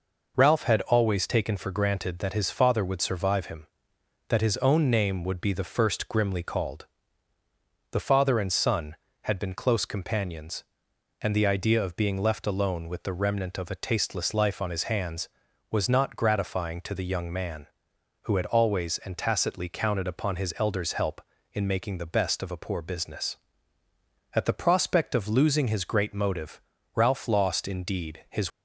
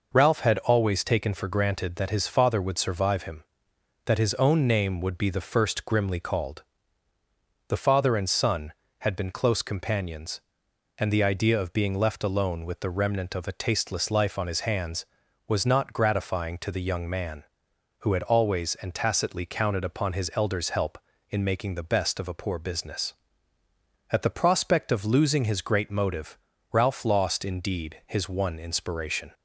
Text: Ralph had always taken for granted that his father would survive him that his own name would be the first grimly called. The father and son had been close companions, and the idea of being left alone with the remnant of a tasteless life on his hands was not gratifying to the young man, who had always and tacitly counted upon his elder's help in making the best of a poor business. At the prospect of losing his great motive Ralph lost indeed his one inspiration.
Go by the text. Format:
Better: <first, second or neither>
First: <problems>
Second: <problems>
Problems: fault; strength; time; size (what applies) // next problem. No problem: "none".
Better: second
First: pauses between "motive" and "Ralph"; slight; at 26.6 s; 0.32 s long // stops before "one inspiration"; at 28.5 s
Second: pauses between "motive" and "Ralph"; slight; at 26.3 s; 0.32 s long